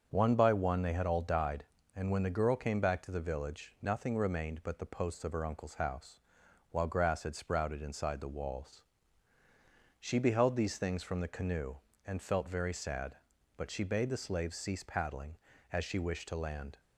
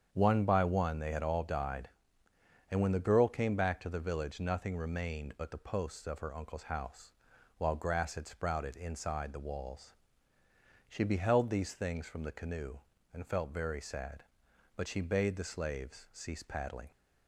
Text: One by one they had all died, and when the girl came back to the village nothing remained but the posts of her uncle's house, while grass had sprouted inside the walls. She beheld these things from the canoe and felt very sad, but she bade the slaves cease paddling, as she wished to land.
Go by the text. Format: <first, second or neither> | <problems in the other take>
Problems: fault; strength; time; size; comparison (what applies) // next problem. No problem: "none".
first | starts louder than the rest; strong; until 1.1 s; 7.5 dB; also in the first // stops before "as she wished to land"; at 16.9 s